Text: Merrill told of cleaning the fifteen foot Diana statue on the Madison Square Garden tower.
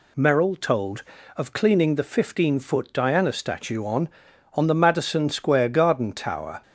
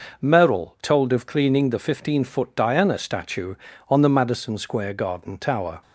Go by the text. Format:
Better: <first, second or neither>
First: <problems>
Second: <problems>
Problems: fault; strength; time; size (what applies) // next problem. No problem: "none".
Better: second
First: says "on" twice; at 4.5 s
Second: none